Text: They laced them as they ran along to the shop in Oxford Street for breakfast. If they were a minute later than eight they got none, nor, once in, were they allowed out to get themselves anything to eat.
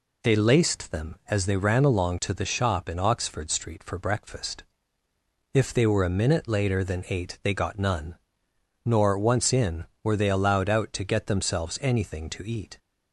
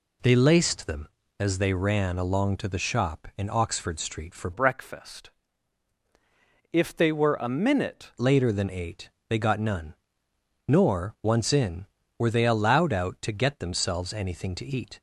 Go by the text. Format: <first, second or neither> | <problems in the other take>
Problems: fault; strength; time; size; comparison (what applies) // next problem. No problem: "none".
first | changes voice from "breakfast" to "minute"; from 4.5 to 8.1 s; 3.6 s long // pauses between "eight" and "they"; slight; at 9.1 s; 0.18 s long